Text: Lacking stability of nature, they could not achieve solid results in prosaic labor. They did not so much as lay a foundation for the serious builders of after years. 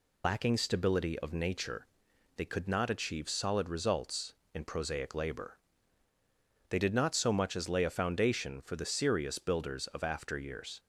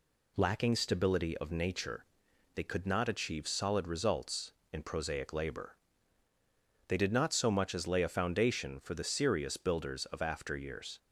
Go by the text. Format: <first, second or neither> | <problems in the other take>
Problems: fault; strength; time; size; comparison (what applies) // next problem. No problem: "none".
second | loses the start of "Lacking"; at 0.2 s; 70 ms